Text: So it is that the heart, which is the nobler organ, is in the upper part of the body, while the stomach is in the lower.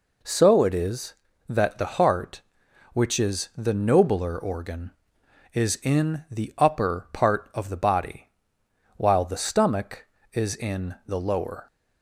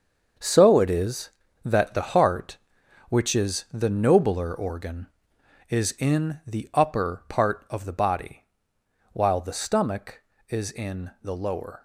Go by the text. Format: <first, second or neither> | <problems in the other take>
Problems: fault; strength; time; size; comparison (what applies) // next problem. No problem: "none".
first | gets quieter; strong; throughout; 10 dB